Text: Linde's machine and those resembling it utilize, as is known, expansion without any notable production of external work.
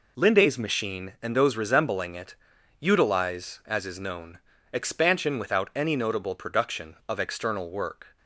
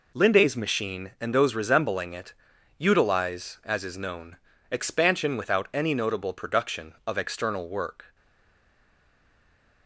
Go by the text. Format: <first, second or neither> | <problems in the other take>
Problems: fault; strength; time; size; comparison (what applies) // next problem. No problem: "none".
first | pauses between "it" and "utilize"; noticeable; at 2.3 s; 0.46 s long; noticeable in the first // stays silent after the last word; noticeable; from 8.1 s on; 1.7 s long